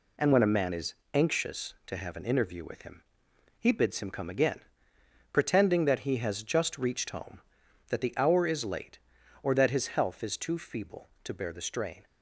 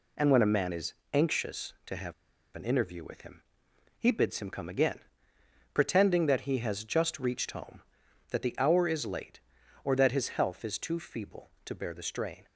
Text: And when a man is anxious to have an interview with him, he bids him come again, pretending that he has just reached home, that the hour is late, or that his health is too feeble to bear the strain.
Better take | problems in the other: first | pauses between "is" and "anxious"; slight; at 0.9 s; 0.20 s long; slight in the first // pauses between "have" and "an"; at 2.1 s; 0.41 s long

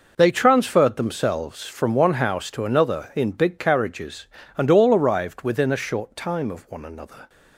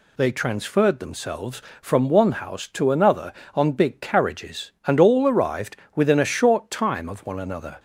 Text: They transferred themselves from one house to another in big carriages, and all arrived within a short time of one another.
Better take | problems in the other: first | says "on" for "in"; at 3.5 s // pauses between "arrived" and "within"; slight; at 5.7 s; 0.18 s long

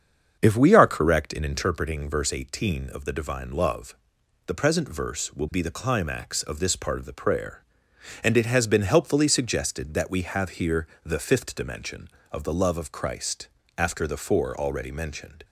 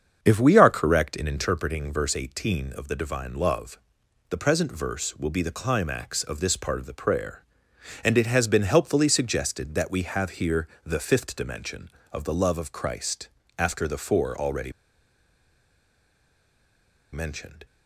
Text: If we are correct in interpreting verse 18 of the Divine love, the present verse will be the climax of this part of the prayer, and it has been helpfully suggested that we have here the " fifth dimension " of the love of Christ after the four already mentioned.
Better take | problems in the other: first | starts louder than the rest; strong; until 1.2 s; 7 dB; strong in the first // pauses between "here" and "the"; slight; at 10.6 s; 0.18 s long; slight in the first // pauses between "Christ" and "after"; slight; at 13.2 s; 0.28 s long; slight in the first // pauses between "already" and "mentioned"; strong; at 14.7 s; 2.4 s long

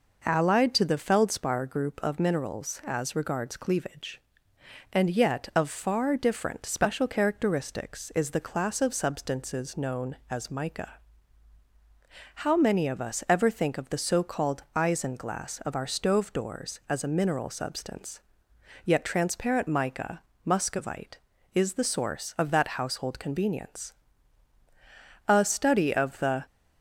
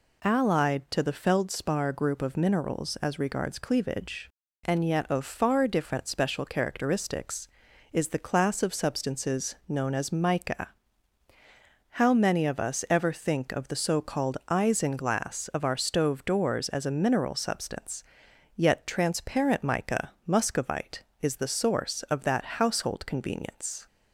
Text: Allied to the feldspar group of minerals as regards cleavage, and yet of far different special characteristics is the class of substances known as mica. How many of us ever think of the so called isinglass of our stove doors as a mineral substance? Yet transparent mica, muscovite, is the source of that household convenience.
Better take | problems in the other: second | goes on to say "A study of the"; noticeable; from 25.2 s on; 1.1 s long

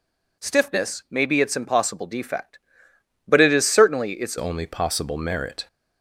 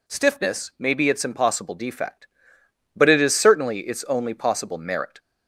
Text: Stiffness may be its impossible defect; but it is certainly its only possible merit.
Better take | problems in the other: second | changes voice at "only"; from 4.3 s on; 1.3 s long

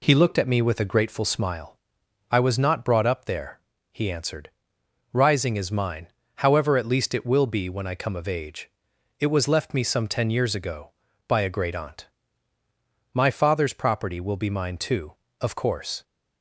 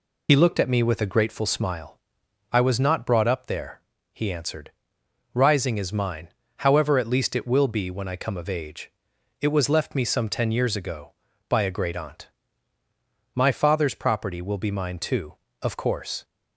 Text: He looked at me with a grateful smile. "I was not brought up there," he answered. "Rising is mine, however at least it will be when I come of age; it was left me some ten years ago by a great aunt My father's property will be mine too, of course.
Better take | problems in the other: first | loses the start of "He"; at 0.2 s; 60 ms // pauses between "aunt" and "My"; at 12.2 s; 1.0 s long; also in the first

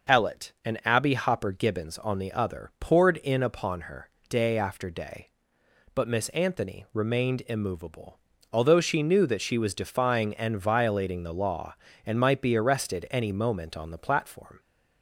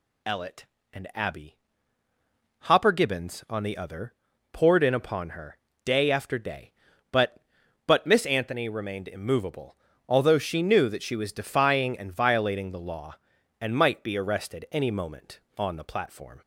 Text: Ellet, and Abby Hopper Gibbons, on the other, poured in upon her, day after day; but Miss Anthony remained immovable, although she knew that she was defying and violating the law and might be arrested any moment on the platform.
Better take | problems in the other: first | pauses between "Abby" and "Hopper"; at 1.5 s; 1.0 s long // says "but" twice; at 7.8 s

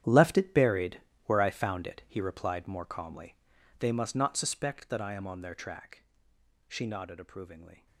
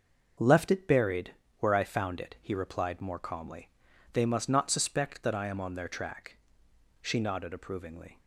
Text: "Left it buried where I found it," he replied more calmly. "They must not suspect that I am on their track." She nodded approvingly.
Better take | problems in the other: second | gets quieter; strong; throughout; 14.5 dB // starts louder than the rest; strong; until 1.3 s; 10 dB; noticeable in the second // pauses between "buried" and "where"; slight; at 0.9 s; 0.24 s long; slight in the second

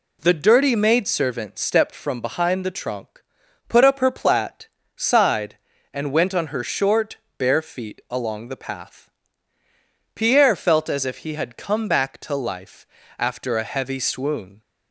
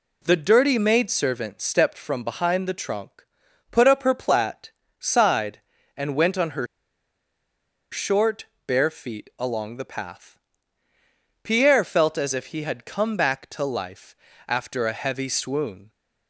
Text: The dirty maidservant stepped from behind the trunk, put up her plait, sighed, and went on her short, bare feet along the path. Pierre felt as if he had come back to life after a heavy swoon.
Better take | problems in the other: first | pauses between "her" and "short"; strong; at 6.6 s; 1.2 s long // pauses between "life" and "after"; slight; at 14.1 s; 0.32 s long; slight in the first

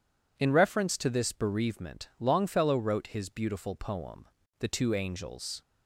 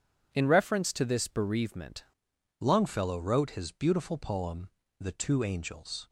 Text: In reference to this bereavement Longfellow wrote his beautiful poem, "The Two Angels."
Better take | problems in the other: first | changes voice at "Longfellow"; from 2.5 s on; 3.5 s long

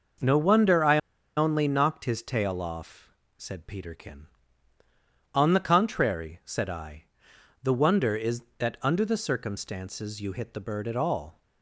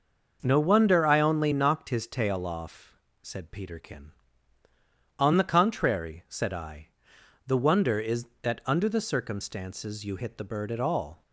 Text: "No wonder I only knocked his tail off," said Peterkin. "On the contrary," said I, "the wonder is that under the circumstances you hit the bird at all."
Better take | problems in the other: second | pauses between "I" and "only"; at 0.9 s; 0.37 s long

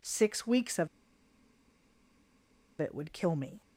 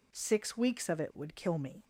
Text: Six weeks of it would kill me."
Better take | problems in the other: second | pauses between "of" and "it"; strong; at 0.8 s; 1.9 s long

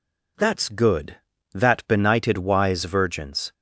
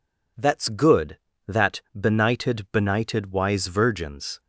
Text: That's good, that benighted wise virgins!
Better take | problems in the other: first | says "benighted" twice; at 2.7 s

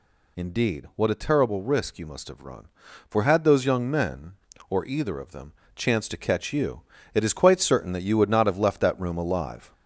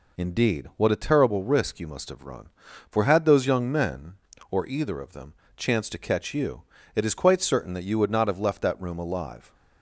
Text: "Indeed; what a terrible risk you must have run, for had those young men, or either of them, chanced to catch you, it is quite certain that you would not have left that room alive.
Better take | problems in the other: second | gets louder; noticeable; throughout; 4 dB

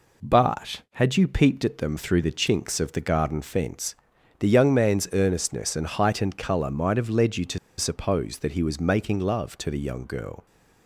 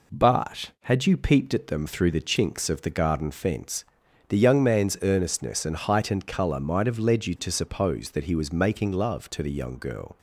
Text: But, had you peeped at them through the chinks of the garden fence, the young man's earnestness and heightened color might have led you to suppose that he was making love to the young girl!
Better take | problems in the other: second | pauses between "to" and "suppose"; slight; at 7.5 s; 0.21 s long

